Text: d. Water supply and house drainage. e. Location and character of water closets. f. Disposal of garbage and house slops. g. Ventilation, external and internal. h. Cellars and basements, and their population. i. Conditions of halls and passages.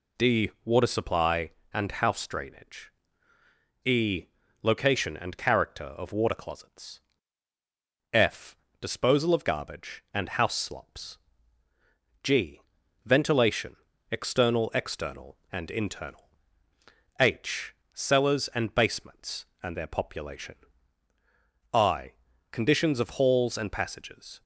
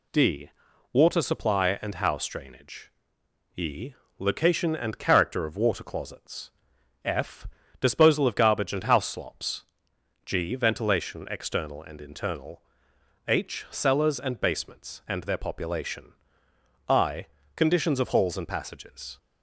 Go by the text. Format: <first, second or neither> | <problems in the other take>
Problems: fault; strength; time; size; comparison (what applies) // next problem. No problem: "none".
second | says "external" twice; at 14.7 s